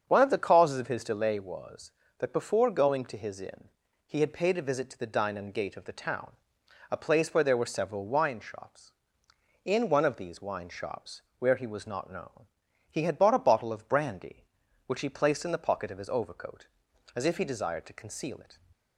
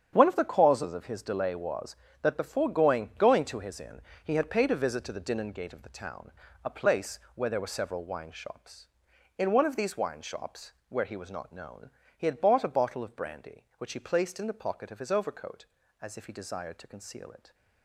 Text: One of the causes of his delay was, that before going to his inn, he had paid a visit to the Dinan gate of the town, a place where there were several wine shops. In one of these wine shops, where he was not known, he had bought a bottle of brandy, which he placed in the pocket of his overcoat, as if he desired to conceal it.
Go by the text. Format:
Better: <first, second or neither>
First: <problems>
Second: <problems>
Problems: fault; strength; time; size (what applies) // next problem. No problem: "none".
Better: first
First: starts louder than the rest; until 1.0 s; 7 dB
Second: starts louder than the rest; strong; until 1.1 s; 8 dB // says "going" twice; at 3.1 s // pauses between "place" and "where"; slight; at 7.1 s; 0.16 s long